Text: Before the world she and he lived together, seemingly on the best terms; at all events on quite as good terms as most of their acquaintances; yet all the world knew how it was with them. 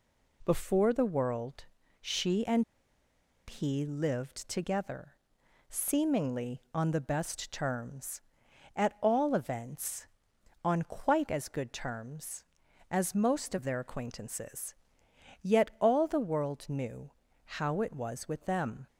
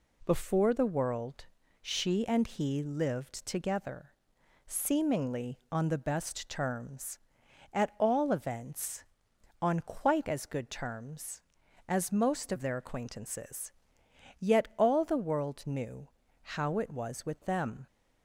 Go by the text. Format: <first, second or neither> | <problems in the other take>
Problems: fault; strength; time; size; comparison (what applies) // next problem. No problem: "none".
second | pauses between "world" and "she"; slight; at 1.6 s; 0.36 s long; slight in the second // pauses between "and" and "he"; noticeable; at 2.6 s; 0.84 s long // pauses between "knew" and "how"; noticeable; at 17.1 s; 0.46 s long; noticeable in the second